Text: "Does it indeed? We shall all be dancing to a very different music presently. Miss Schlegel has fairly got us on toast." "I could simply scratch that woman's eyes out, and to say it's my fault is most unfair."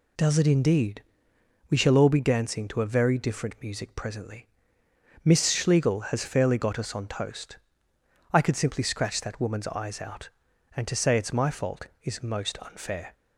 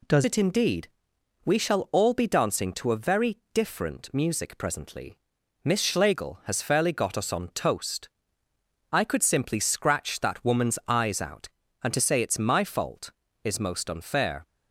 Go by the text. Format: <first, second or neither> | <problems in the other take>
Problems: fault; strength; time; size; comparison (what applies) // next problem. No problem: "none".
first | changes voice at "it"; from 0.2 s on; 14.2 s long